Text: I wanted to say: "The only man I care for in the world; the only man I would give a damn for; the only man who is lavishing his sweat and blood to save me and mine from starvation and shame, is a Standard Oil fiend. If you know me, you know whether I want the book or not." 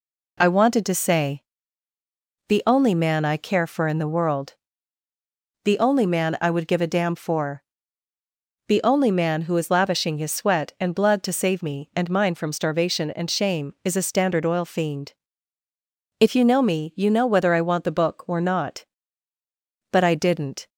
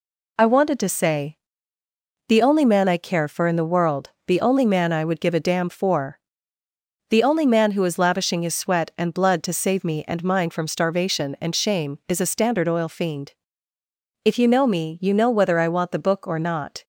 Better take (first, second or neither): second